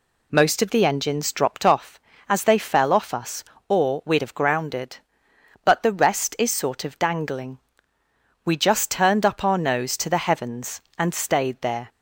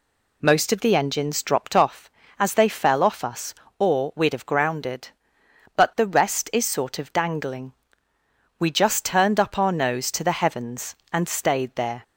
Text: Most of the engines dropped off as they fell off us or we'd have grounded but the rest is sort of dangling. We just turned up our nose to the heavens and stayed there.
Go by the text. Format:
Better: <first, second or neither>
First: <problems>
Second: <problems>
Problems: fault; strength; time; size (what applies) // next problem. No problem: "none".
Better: neither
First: none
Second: none